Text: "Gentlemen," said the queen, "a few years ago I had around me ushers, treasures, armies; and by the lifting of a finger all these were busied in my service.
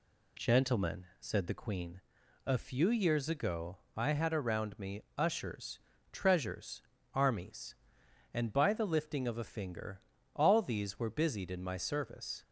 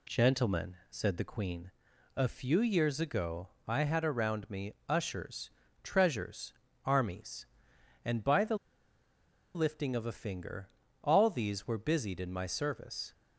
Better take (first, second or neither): first